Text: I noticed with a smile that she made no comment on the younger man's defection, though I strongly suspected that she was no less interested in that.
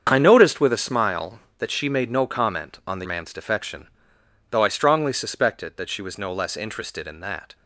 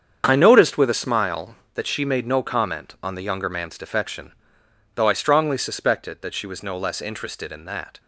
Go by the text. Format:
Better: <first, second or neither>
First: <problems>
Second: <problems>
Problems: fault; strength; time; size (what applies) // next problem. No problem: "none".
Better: second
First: starts louder than the rest; strong; until 1.1 s; 7.5 dB // skips "younger"; at 3.0 s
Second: starts louder than the rest; strong; until 1.2 s; 7.5 dB